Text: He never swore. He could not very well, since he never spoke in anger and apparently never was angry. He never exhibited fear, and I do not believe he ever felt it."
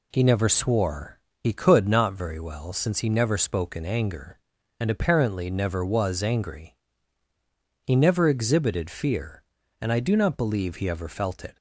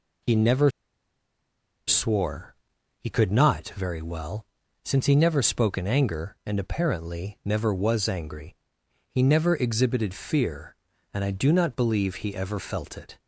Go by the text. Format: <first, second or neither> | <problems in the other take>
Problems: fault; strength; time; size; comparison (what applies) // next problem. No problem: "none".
first | pauses between "never" and "swore"; at 0.7 s; 1.1 s long